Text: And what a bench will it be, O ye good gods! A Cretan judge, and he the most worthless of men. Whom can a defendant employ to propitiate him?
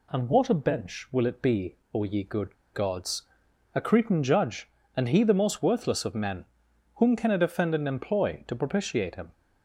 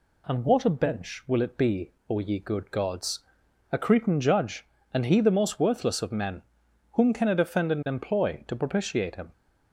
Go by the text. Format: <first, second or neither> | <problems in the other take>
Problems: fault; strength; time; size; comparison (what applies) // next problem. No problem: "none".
second | pauses between "good" and "gods"; slight; at 2.5 s; 0.19 s long